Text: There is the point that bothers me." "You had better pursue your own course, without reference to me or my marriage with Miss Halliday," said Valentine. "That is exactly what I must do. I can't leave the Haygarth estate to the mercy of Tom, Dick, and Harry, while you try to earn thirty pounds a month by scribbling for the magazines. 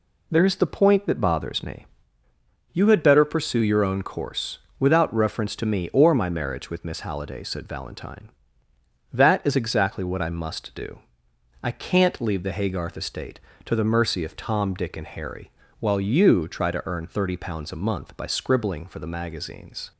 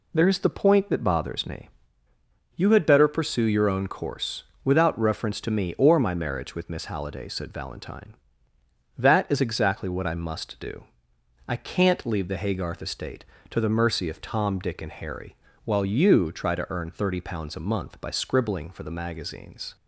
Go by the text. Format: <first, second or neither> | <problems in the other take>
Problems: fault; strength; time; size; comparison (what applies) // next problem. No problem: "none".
neither | none